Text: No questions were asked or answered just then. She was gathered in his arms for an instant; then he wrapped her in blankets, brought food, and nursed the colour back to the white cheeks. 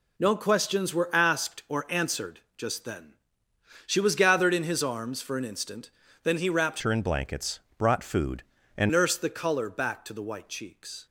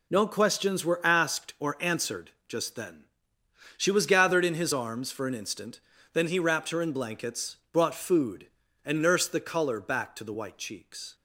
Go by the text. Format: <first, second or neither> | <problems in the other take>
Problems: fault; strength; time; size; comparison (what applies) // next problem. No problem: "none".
second | pauses between "answered" and "just"; slight; at 2.3 s; 0.18 s long; slight in the second // changes voice from "her" to "and"; from 6.8 to 8.8 s; 2.0 s long